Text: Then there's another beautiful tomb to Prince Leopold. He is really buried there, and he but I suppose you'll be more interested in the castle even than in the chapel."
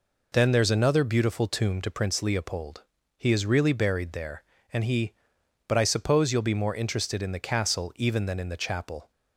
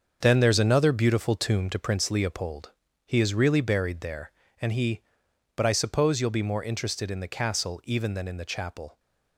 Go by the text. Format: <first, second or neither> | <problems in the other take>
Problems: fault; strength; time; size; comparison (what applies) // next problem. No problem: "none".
first | gets quieter; strong; throughout; 9.5 dB